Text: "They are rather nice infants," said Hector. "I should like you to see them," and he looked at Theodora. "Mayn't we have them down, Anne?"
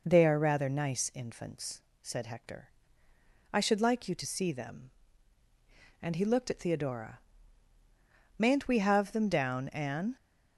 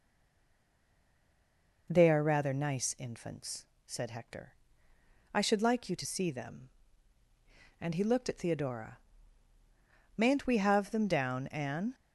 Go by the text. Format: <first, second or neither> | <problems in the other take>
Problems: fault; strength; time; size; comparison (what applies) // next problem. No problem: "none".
first | stays silent before the first word; noticeable; until 1.8 s; 1.8 s long